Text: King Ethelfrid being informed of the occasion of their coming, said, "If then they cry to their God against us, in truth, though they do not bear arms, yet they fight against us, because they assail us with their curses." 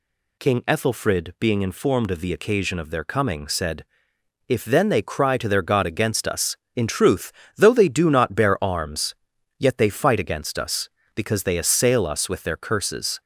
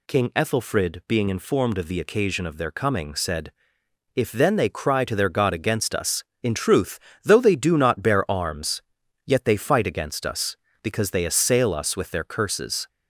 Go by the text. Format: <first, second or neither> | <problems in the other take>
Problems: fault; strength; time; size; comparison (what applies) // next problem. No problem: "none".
neither | none